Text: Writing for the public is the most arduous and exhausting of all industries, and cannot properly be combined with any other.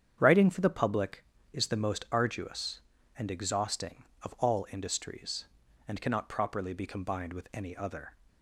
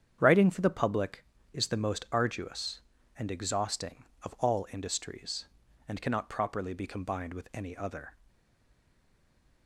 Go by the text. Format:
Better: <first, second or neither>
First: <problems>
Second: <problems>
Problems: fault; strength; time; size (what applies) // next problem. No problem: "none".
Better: first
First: starts louder than the rest; strong; until 1.2 s; 8.5 dB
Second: starts louder than the rest; strong; until 1.2 s; 8.5 dB // stays silent after the last word; noticeable; from 8.2 s on; 1.4 s long